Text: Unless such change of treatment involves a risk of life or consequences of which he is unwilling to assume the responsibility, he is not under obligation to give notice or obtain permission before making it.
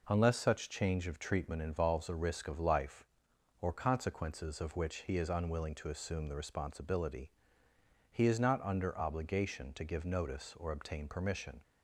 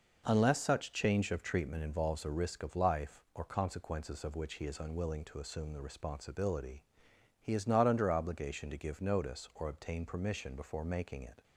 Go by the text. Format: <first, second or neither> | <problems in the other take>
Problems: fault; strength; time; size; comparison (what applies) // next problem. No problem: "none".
second | stops before "before making it"; at 11.6 s